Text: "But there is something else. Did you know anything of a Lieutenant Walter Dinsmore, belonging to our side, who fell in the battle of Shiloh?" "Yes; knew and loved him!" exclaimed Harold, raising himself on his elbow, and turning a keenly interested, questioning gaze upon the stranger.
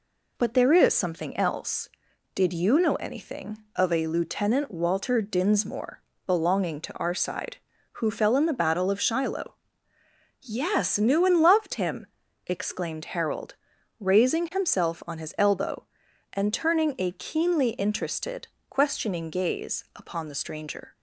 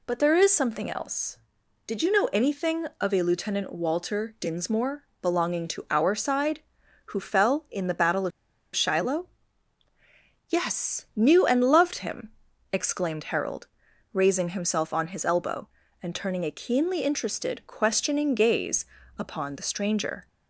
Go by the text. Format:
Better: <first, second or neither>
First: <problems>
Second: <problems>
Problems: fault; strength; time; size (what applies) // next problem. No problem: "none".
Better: first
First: none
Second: pauses between "of" and "Shiloh"; at 8.3 s; 0.44 s long // pauses between "gaze" and "upon"; slight; at 18.8 s; 0.32 s long